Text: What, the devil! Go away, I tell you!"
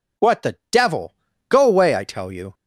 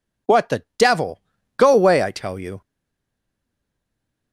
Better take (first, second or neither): first